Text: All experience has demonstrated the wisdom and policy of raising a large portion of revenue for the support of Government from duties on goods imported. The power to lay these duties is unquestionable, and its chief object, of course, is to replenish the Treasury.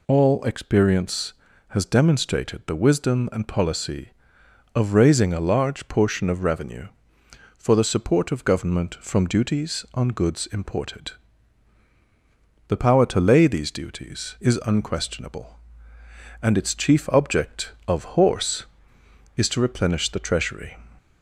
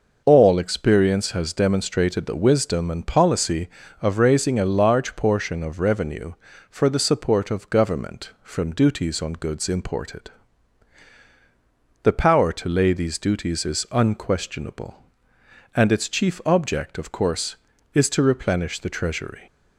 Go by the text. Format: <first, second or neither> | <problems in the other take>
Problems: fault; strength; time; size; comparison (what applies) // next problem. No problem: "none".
second | says "horse" for "course"; at 18.0 s